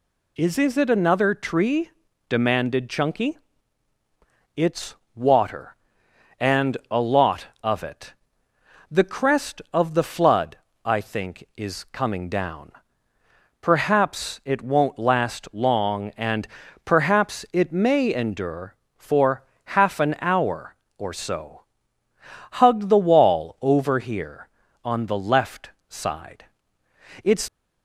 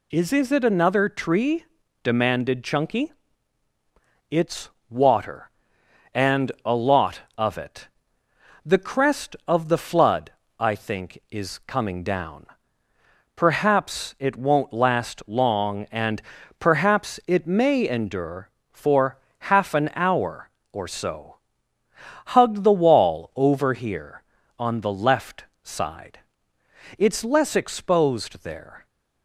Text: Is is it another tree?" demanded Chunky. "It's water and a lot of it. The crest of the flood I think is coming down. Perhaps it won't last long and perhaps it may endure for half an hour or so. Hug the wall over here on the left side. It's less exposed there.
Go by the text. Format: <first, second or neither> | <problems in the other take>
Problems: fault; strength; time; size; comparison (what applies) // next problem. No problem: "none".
second | pauses between "It's" and "water"; slight; at 4.9 s; 0.18 s long; slight in the second // pauses between "flood" and "I"; slight; at 10.5 s; 0.30 s long; slight in the second // pauses between "and" and "perhaps"; at 16.4 s; 0.38 s long; also in the second // pauses between "for" and "half"; slight; at 19.4 s; 0.32 s long; slight in the second // pauses between "left" and "side"; slight; at 25.7 s; 0.18 s long; slight in the second // stops before "less exposed there"; at 27.4 s